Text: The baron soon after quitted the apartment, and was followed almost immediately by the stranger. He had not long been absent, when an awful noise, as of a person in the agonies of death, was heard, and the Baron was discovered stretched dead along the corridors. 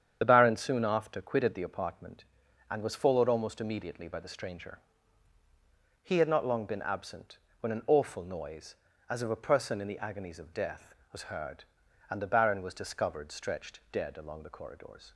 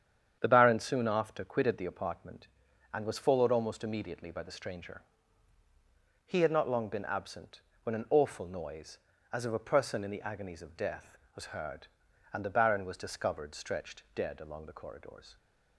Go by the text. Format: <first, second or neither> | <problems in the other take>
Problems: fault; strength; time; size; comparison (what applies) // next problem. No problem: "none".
second | loses the start of "The"; at 0.2 s; 40 ms // starts louder than the rest; strong; until 1.2 s; 8.5 dB; strong in the second